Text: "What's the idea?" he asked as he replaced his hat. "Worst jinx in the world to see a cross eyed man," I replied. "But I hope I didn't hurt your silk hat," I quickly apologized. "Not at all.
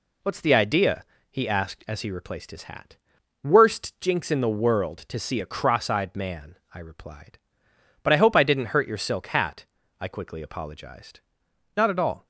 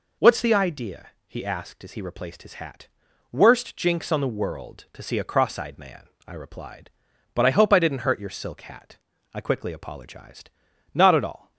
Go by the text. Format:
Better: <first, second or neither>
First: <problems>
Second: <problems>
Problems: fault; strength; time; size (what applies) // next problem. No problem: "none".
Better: first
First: none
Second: says "on" for "in"; at 4.1 s